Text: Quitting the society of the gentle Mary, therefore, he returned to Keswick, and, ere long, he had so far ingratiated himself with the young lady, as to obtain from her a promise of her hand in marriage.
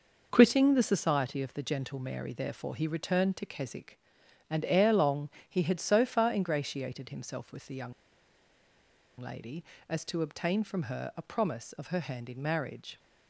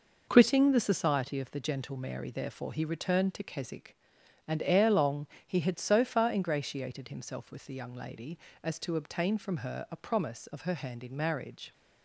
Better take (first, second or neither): second